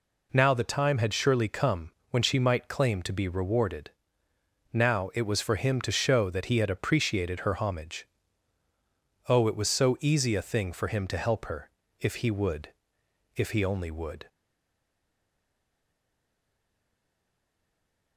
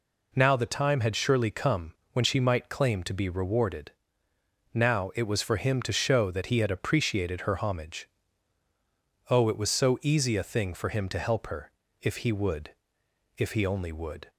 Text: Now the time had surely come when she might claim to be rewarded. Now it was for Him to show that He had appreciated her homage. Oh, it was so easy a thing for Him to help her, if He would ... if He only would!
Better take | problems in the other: second | pauses between "come" and "when"; slight; at 1.9 s; 0.20 s long; slight in the second // stays silent after the last word; strong; from 14.2 s on; 3.9 s long

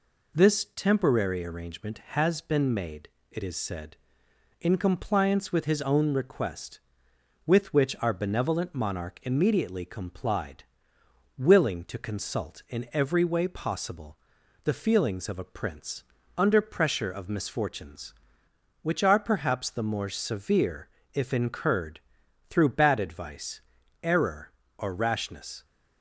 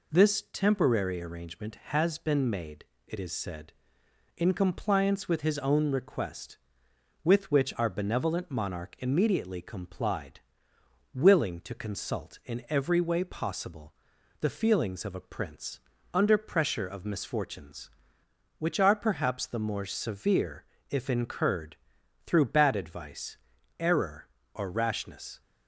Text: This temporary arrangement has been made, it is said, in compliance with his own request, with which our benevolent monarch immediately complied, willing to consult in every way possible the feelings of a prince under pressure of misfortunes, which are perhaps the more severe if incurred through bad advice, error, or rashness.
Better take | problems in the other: neither | pauses between "possible" and "the"; noticeable; the same in both // pauses between "prince" and "under"; slight; the same in both // pauses between "severe" and "if"; slight; the same in both // pauses between "incurred" and "through"; noticeable; the same in both

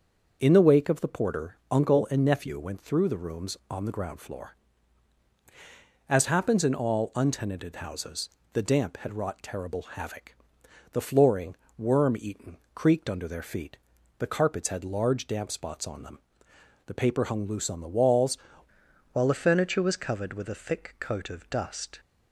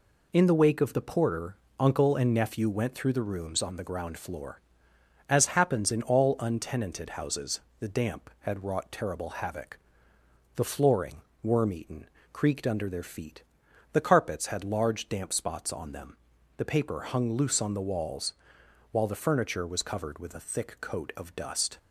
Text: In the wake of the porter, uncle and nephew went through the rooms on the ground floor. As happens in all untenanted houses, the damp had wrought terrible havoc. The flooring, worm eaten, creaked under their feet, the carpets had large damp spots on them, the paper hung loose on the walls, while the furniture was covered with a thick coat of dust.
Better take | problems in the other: second | starts louder than the rest; until 1.4 s; 6.5 dB // changes voice at "while"; from 19.1 s on; 2.8 s long

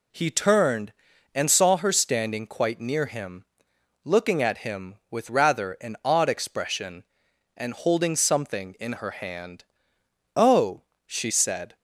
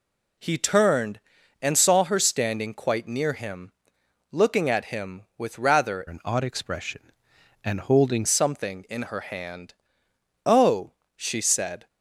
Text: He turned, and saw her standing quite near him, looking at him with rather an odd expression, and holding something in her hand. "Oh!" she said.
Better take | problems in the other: first | changes voice from "an" to "holding"; from 6.0 to 8.2 s; 2.2 s long

